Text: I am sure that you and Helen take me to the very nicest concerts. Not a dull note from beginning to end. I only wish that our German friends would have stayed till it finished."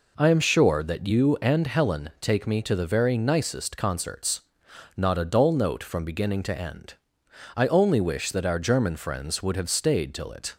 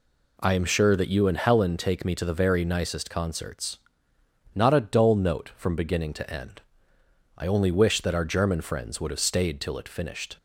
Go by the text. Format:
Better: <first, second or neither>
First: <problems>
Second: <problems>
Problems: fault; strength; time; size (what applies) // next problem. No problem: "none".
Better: second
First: stops before "finished"; at 10.5 s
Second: none